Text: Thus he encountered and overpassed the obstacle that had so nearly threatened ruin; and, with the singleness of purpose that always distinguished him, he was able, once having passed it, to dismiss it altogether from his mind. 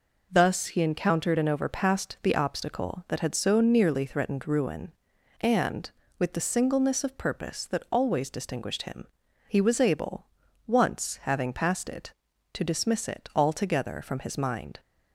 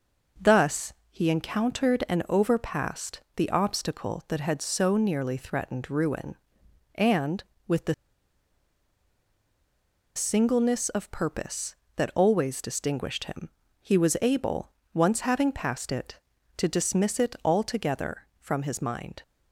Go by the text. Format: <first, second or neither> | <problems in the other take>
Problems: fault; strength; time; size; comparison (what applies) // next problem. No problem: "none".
first | pauses between "Thus" and "he"; slight; at 0.9 s; 0.18 s long // pauses between "overpassed" and "the"; slight; at 3.2 s; 0.16 s long // pauses between "the" and "singleness"; strong; at 7.9 s; 2.2 s long